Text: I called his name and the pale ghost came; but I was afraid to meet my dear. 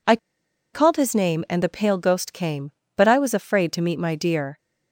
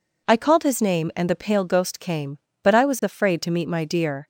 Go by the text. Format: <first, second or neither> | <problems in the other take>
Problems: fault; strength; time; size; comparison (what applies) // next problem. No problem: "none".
second | pauses between "I" and "called"; noticeable; at 0.1 s; 0.56 s long